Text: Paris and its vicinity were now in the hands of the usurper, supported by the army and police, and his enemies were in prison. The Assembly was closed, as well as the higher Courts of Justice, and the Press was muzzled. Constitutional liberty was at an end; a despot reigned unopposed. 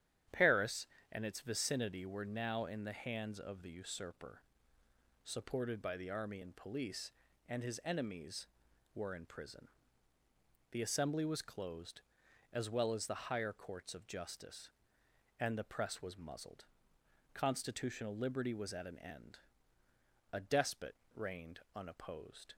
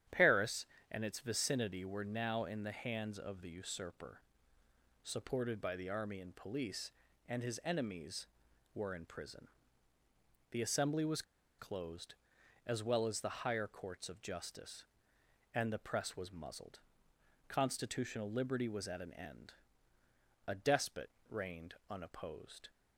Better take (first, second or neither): first